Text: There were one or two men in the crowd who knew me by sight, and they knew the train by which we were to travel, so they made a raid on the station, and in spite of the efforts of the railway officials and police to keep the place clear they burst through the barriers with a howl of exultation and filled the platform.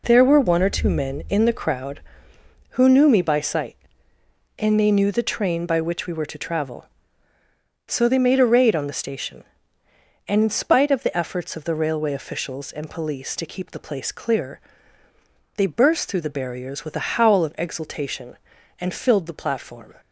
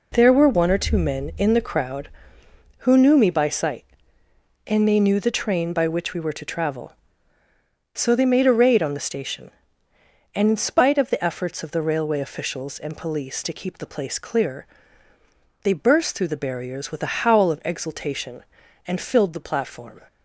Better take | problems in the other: neither | pauses between "clear" and "they"; noticeable; the same in both

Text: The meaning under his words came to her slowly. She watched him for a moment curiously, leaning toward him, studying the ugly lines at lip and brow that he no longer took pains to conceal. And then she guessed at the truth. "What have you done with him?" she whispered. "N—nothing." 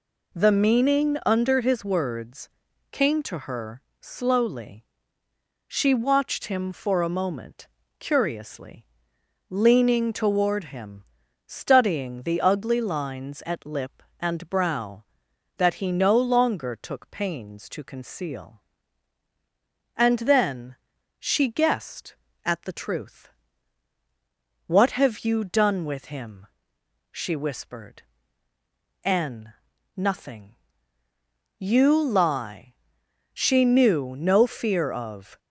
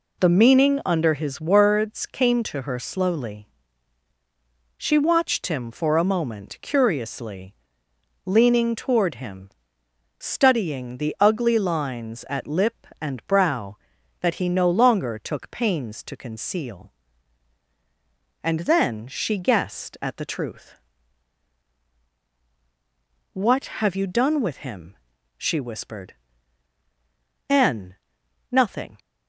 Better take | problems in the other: second | pauses between "words" and "came"; at 2.4 s; 0.42 s long // pauses between "her" and "slowly"; slight; at 3.8 s; 0.18 s long // pauses between "moment" and "curiously"; slight; at 7.6 s; 0.32 s long // pauses between "then" and "she"; at 20.7 s; 0.44 s long // goes on to say "You lie She knew no fear of"; strong; from 31.5 s on; 3.8 s long

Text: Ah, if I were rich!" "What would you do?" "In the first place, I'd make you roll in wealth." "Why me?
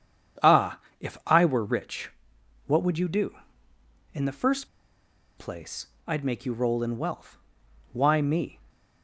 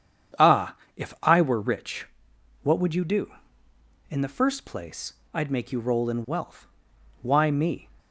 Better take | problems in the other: second | starts louder than the rest; strong; until 1.7 s; 8 dB; strong in the second // pauses between "first" and "place"; noticeable; at 4.6 s; 0.70 s long

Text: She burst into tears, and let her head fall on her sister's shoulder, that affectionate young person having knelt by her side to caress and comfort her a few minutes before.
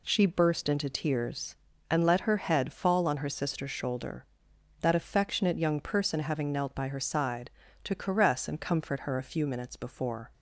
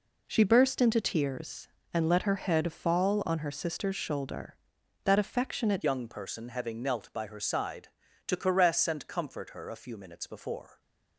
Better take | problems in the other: first | changes voice at "young"; from 5.8 s on; 5.0 s long

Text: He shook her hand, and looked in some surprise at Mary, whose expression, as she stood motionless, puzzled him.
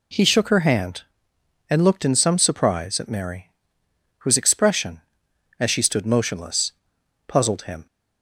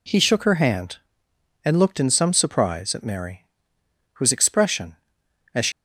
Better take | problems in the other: first | stops before "stood motionless puzzled him"; at 5.7 s

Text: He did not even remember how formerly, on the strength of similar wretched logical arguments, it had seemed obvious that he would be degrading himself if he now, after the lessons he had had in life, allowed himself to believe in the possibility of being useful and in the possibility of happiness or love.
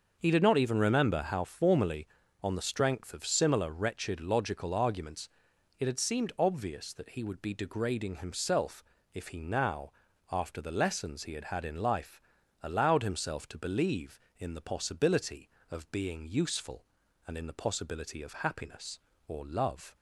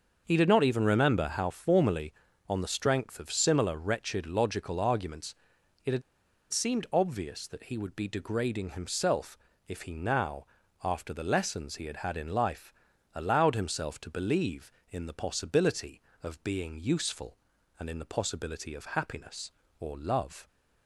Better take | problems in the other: first | starts louder than the rest; until 1.2 s; 6.5 dB; also in the first // pauses between "had" and "seemed"; noticeable; at 6.0 s; 0.49 s long // pauses between "himself" and "if"; slight; at 9.3 s; 0.30 s long; slight in the first

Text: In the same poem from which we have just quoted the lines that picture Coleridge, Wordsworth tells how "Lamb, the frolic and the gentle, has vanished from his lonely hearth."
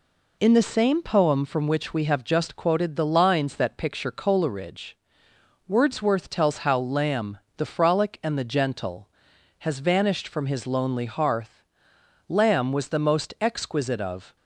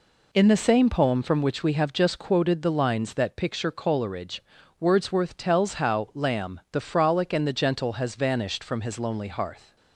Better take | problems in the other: second | goes on to say "Lamb was the most exquisite of"; strong; from 12.2 s on; 2.0 s long

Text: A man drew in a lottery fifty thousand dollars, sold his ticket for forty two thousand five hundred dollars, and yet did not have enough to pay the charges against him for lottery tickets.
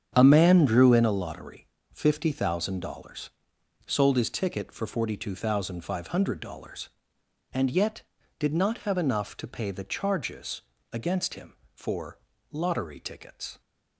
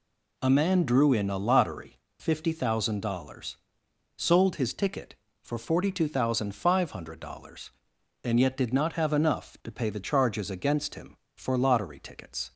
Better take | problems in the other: second | starts louder than the rest; strong; until 1.2 s; 8 dB // pauses between "lottery" and "fifty"; slight; at 1.6 s; 0.26 s long; slight in the second // pauses between "charges" and "against"; slight; at 10.6 s; 0.28 s long // pauses between "for" and "lottery"; slight; at 12.1 s; 0.32 s long

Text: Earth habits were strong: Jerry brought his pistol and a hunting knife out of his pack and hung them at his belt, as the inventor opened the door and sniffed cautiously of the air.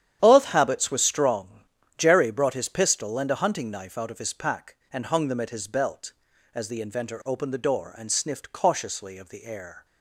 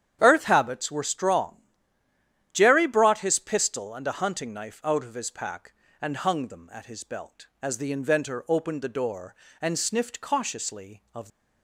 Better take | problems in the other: first | starts louder than the rest; strong; until 1.2 s; 9.5 dB; strong in the first // stops before "the air"; at 11.2 s

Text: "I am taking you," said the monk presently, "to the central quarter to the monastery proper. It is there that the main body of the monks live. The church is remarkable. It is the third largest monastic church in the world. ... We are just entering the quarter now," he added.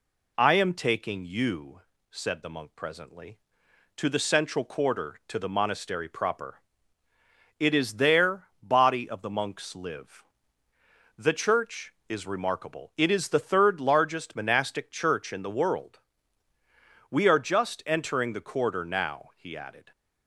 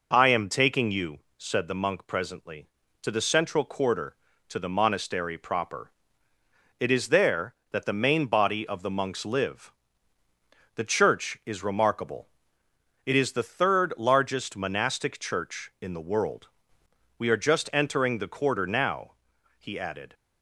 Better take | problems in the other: second | skips "that the main"; at 8.5 s

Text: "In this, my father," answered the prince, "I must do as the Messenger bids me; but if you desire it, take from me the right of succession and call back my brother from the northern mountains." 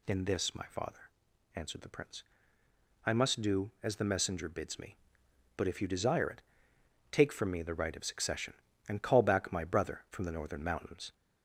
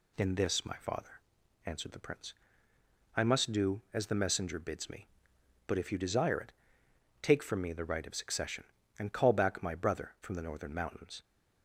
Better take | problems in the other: second | gets louder; slight; throughout; 2.5 dB

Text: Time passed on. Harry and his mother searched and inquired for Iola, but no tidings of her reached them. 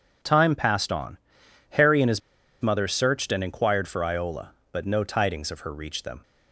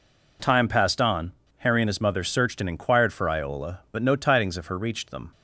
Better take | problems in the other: second | pauses between "his" and "mother"; at 2.2 s; 0.41 s long

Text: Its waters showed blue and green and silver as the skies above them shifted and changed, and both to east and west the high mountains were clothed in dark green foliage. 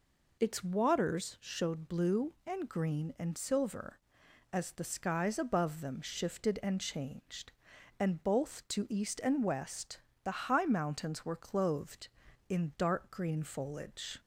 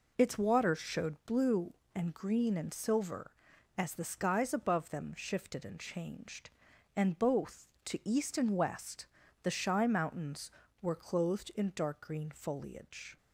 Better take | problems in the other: first | pauses between "west" and "the"; slight; at 9.0 s; 0.36 s long; slight in the first // says "shy" for "high"; at 9.5 s

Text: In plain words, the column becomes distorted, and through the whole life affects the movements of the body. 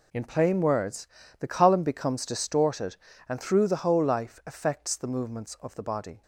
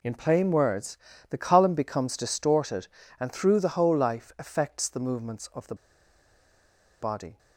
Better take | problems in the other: first | pauses between "the" and "body"; strong; at 5.7 s; 1.2 s long

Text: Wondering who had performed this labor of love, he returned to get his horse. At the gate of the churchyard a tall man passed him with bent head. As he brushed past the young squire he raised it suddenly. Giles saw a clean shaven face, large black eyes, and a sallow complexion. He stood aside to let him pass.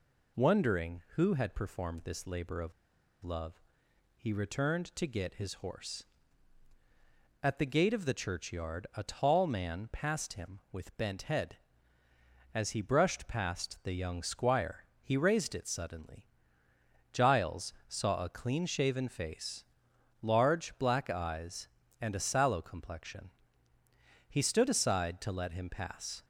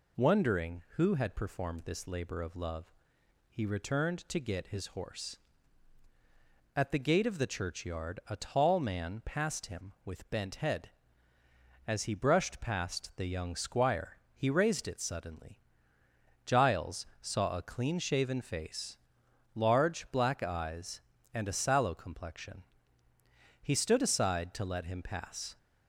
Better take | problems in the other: second | pauses between "of" and "love"; noticeable; at 2.7 s; 0.51 s long // pauses between "squire" and "he"; slight; at 14.8 s; 0.18 s long; slight in the second // pauses between "Giles" and "saw"; slight; at 17.7 s; 0.16 s long; slight in the second

